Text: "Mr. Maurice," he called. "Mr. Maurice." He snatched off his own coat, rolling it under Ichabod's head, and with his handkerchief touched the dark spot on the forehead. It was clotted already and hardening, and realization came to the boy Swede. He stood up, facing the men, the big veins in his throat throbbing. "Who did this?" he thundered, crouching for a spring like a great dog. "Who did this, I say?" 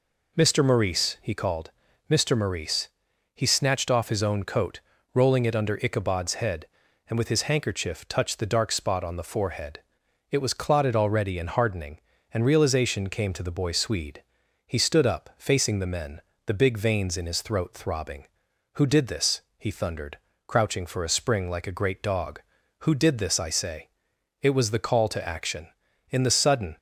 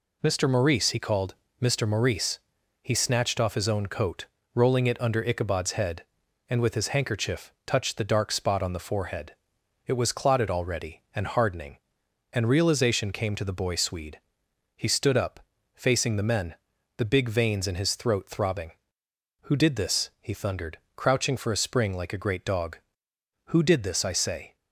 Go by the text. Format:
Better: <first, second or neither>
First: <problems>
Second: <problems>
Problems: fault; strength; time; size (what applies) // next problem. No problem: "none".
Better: second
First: goes on to say "It was the call to action In the sudden"; strong; from 24.4 s on; 2.3 s long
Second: none